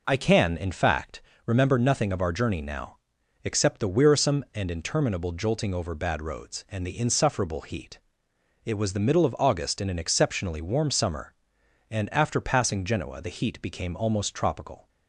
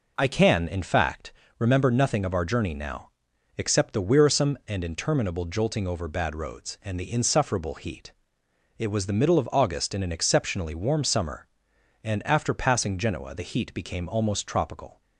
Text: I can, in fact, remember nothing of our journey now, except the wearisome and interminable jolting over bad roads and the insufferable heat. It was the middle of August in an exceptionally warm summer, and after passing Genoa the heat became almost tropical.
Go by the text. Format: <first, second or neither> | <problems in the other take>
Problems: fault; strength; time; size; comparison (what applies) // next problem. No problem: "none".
neither | none